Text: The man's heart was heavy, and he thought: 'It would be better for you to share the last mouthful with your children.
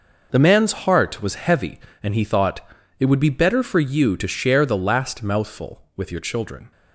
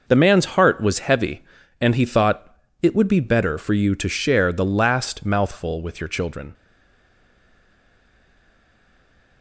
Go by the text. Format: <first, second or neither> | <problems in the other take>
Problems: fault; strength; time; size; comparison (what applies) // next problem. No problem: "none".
first | stays silent after the last word; strong; from 6.5 s on; 2.9 s long